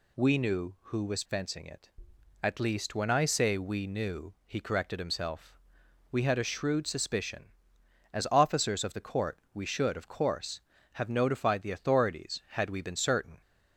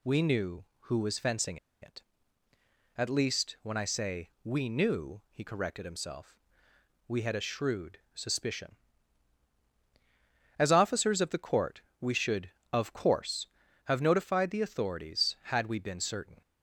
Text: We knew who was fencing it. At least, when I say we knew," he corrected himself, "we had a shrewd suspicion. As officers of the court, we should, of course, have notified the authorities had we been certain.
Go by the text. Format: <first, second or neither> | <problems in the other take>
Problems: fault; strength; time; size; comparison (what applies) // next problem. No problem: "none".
first | pauses between "fencing" and "it"; slight; at 1.5 s; 0.25 s long // pauses between "shrewd" and "suspicion"; slight; at 7.9 s; 0.16 s long